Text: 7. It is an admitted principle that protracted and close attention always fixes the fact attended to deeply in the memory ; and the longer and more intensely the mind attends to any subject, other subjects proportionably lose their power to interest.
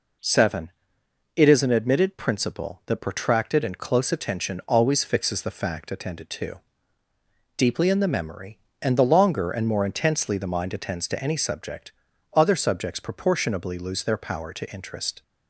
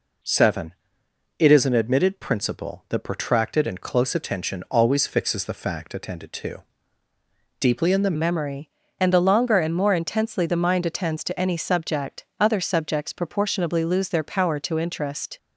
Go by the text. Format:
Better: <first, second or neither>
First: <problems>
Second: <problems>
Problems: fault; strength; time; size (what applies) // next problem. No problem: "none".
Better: first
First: pauses between "to" and "deeply"; noticeable; at 6.5 s; 0.96 s long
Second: pauses between "to" and "deeply"; noticeable; at 6.6 s; 0.96 s long // changes voice at "memory"; from 8.1 s on; 7.2 s long